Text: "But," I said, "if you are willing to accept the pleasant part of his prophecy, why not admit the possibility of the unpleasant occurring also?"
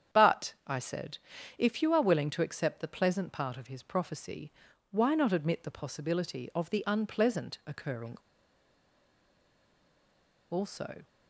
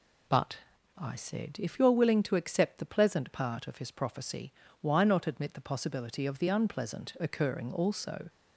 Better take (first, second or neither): second